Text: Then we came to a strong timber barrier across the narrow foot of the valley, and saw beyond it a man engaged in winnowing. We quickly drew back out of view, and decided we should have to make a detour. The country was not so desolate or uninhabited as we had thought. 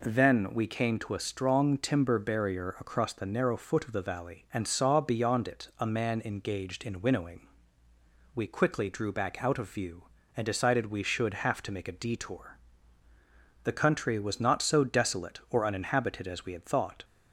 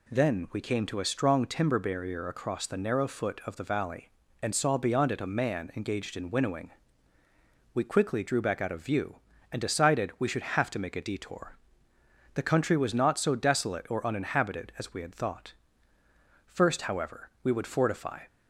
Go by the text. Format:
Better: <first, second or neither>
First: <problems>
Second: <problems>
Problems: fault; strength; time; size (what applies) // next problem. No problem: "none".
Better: first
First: none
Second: goes on to say "First however we would fortify"; strong; from 16.4 s on; 1.7 s long